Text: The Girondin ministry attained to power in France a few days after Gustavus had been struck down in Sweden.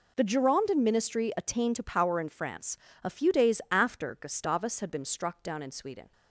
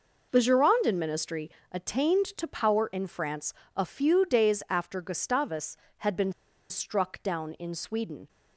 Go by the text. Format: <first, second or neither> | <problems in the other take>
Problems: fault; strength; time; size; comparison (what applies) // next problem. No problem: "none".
first | pauses between "ministry" and "attained"; slight; at 1.4 s; 0.22 s long // pauses between "France" and "a"; slight; at 3.5 s; 0.24 s long; slight in the first // pauses between "been" and "struck"; at 6.3 s; 0.37 s long